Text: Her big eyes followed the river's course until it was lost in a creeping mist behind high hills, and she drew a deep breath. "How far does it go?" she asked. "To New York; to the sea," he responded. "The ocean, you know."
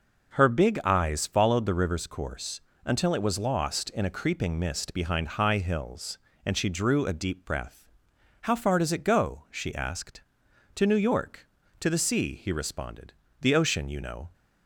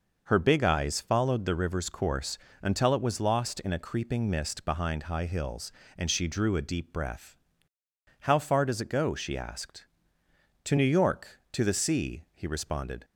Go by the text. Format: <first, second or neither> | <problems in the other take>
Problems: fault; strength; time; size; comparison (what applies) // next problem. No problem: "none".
first | pauses between "course" and "until"; slight; at 2.3 s; 0.24 s long; slight in the first // stops before "The ocean you know"; at 13.0 s